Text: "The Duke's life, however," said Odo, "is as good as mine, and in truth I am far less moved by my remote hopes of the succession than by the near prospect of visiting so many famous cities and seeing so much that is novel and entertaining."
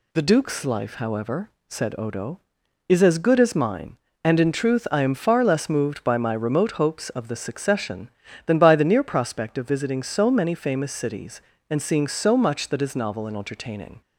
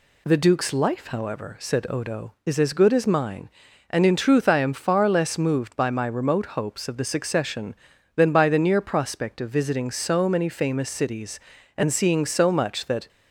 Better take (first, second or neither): first